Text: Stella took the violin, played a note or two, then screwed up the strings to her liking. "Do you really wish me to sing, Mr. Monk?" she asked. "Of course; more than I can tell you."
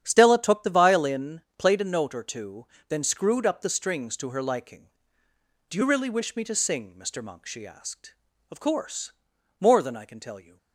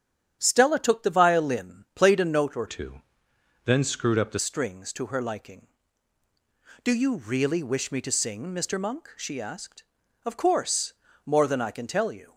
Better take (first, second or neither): first